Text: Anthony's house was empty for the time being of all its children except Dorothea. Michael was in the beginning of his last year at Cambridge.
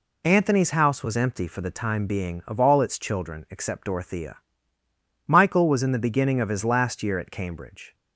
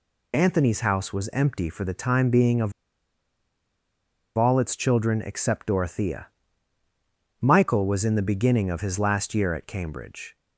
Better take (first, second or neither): first